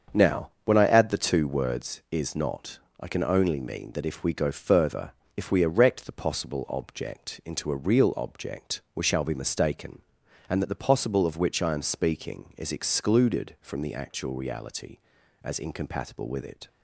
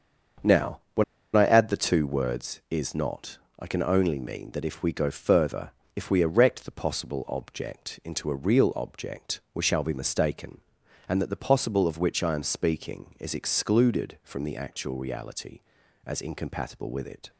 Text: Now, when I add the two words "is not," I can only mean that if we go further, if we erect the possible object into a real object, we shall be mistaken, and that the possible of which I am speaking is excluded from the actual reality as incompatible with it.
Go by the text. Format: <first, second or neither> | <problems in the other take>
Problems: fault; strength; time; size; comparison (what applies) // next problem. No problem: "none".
first | starts louder than the rest; until 1.9 s; 6.5 dB; also in the first // pauses between "when" and "I"; slight; at 1.0 s; 0.32 s long